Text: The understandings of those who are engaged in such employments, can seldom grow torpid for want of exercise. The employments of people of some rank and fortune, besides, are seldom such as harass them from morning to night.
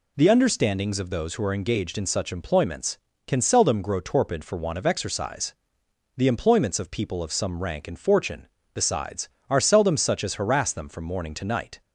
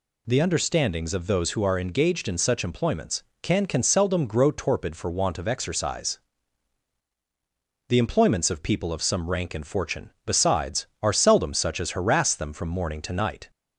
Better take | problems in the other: first | says "can" twice; at 3.6 s

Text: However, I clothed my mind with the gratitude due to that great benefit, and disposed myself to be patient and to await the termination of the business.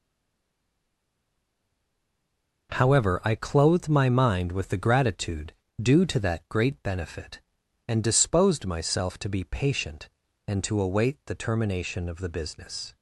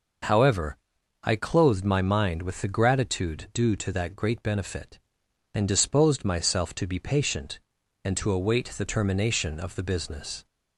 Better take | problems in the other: second | stays silent before the first word; strong; until 2.6 s; 2.6 s long // pauses between "gratitude" and "due"; slight; at 5.5 s; 0.28 s long

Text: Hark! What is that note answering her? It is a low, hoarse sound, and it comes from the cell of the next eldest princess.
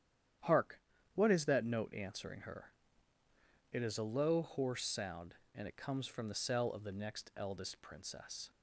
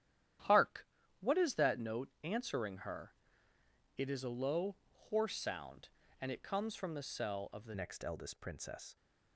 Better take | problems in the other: first | starts louder than the rest; strong; until 1.7 s; 11 dB; strong in the first // changes voice at "next"; from 7.7 s on; 1.2 s long

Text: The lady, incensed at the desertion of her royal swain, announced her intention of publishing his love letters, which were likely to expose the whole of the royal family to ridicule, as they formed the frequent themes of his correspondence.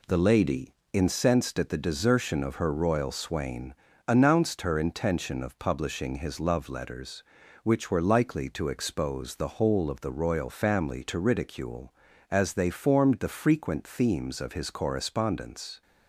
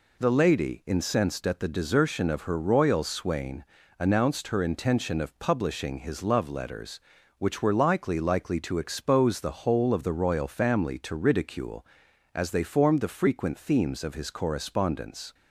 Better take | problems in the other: first | says "likely" twice; at 8.1 s

